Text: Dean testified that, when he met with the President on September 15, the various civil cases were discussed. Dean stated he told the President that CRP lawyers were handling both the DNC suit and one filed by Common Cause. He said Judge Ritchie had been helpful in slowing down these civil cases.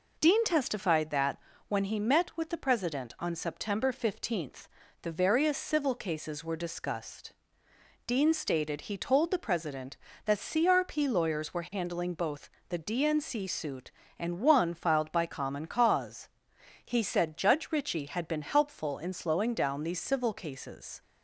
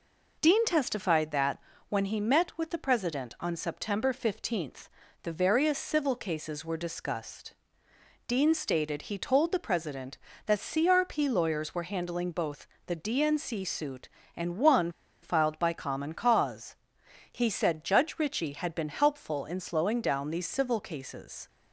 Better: first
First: pauses between "both" and "the"; slight; at 12.5 s; 0.18 s long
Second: pauses between "both" and "the"; slight; at 12.6 s; 0.18 s long // pauses between "one" and "filed"; slight; at 14.9 s; 0.30 s long

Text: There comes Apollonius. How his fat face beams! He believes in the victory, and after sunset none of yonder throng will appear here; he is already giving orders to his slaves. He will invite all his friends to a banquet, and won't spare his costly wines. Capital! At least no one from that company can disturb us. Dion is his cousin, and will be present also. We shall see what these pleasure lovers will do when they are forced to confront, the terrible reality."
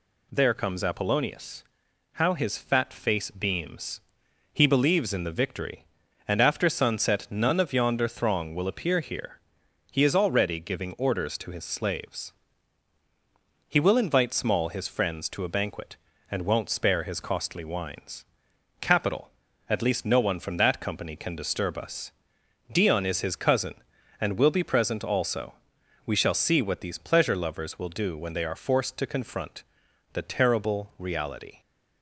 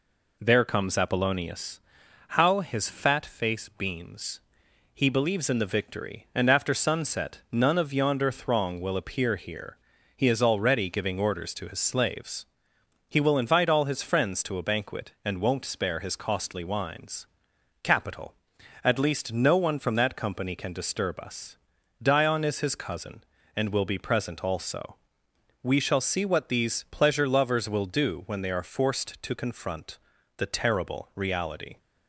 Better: second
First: says "small" for "all"; at 14.3 s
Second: none

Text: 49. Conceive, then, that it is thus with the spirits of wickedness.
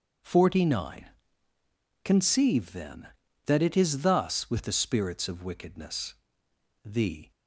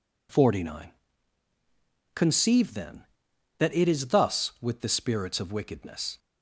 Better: second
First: starts louder than the rest; until 2.1 s; 6.5 dB // goes on to say "The"; slight; from 6.8 s on; 0.46 s long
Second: none

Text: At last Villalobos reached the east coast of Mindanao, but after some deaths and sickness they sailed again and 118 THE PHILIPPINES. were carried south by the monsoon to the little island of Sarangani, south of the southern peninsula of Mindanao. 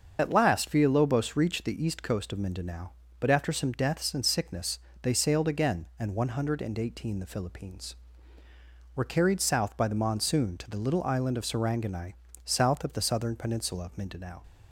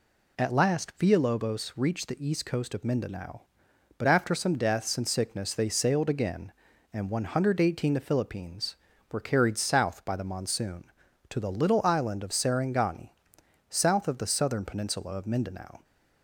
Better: second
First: loses the start of "At"; at 0.1 s; 40 ms // starts louder than the rest; until 1.2 s; 6.5 dB // pauses between "sickness" and "they"; slight; at 4.7 s; 0.24 s long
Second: none

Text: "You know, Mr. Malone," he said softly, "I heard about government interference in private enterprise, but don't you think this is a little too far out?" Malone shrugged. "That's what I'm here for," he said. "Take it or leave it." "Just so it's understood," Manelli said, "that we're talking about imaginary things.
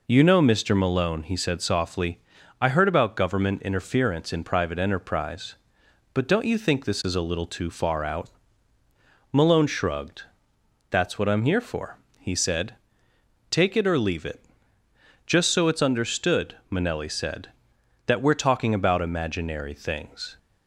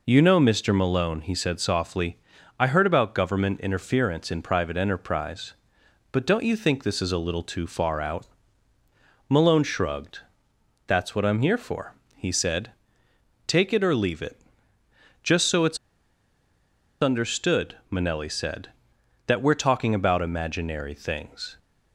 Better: first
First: none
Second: pauses between "it's" and "understood"; at 15.7 s; 1.2 s long

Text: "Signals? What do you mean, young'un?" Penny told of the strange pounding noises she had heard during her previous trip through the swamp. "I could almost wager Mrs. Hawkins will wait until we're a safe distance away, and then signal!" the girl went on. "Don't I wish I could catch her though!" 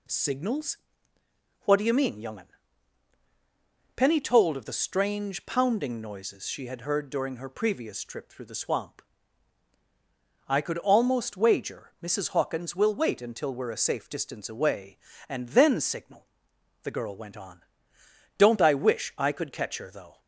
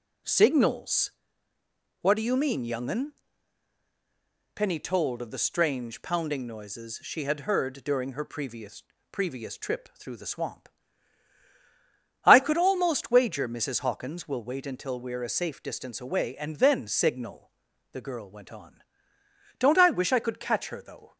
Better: first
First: none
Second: says "previous" twice; at 9.1 s

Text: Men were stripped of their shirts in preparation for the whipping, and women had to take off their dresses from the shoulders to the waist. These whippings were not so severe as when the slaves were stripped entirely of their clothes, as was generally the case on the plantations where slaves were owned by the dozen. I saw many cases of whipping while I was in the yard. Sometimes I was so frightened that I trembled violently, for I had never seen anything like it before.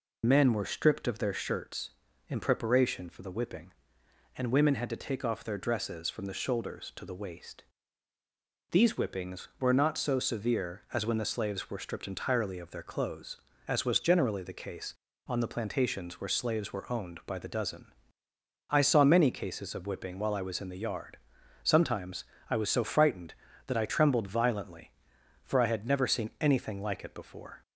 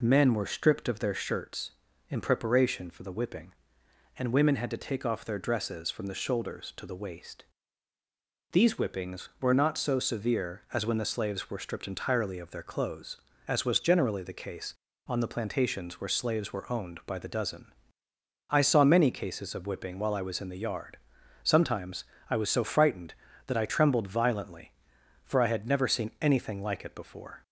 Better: second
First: loses the start of "Men"; at 0.2 s; 40 ms // pauses between "Sometimes" and "I"; slight; at 22.2 s; 0.26 s long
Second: pauses between "Sometimes" and "I"; slight; at 22.0 s; 0.26 s long

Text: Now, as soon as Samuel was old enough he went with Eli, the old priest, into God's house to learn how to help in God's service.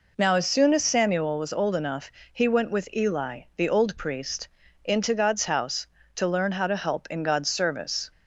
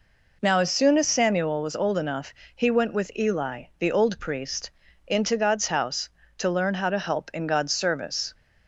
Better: neither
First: pauses between "enough" and "he"; slight; at 2.1 s; 0.20 s long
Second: pauses between "enough" and "he"; slight; at 2.3 s; 0.20 s long

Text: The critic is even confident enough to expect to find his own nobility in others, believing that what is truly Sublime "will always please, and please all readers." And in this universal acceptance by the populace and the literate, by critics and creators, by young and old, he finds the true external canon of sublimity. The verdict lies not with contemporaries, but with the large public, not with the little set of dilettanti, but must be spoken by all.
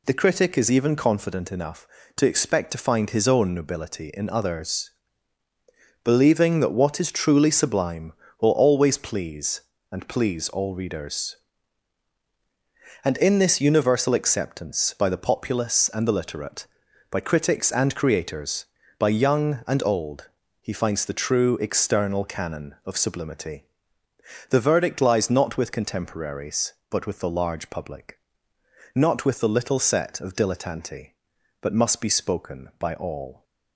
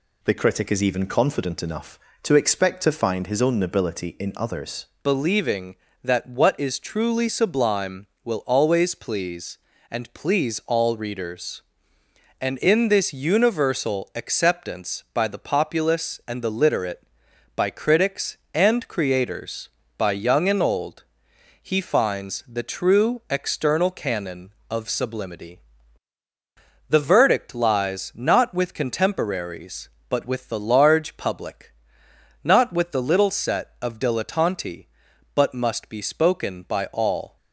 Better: first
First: none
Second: changes voice at "believing"; from 5.0 s on; 32.3 s long

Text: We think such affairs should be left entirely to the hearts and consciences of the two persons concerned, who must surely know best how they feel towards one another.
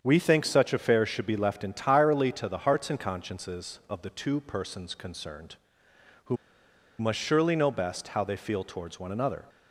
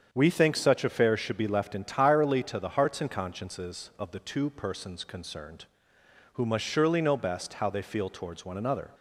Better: second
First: starts louder than the rest; strong; until 1.0 s; 7.5 dB // pauses between "who" and "must"; noticeable; at 6.3 s; 0.64 s long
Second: starts louder than the rest; strong; until 1.1 s; 7.5 dB

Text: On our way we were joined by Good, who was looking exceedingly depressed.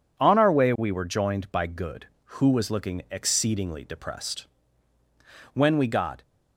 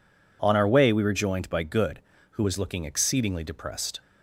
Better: second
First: goes on to say "When we got"; noticeable; from 5.5 s on; 0.68 s long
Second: none

